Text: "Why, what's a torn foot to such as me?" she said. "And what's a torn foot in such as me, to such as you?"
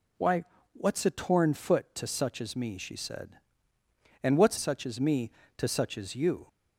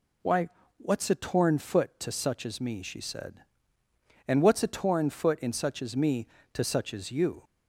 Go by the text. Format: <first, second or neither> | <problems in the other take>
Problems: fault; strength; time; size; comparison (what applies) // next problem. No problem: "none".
second | skips "a torn foot in"; at 4.5 s